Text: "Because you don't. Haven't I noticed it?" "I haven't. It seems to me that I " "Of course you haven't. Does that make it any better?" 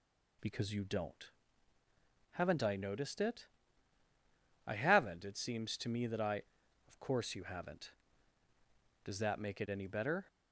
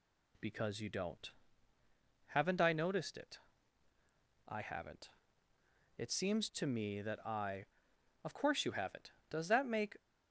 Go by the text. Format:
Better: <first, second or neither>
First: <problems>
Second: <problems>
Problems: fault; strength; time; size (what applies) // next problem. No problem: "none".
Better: first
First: none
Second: stops before "it any better"; at 9.9 s